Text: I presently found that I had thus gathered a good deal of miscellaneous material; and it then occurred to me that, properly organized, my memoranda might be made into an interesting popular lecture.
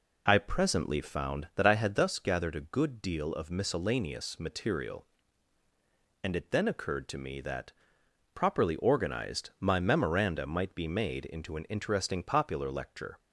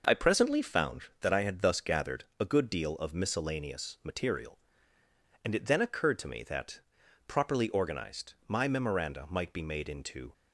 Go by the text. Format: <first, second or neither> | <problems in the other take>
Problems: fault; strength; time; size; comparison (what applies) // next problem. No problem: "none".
first | stops before "an interesting popular lecture"; at 10.3 s